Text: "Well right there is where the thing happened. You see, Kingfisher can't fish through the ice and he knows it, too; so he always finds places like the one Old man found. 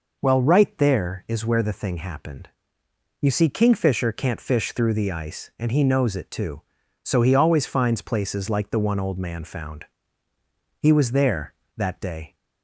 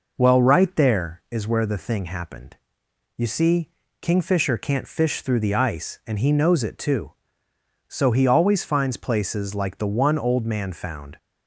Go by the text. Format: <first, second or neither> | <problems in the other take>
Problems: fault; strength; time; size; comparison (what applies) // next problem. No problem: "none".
second | goes on to say "He was there that day"; from 10.8 s on; 1.5 s long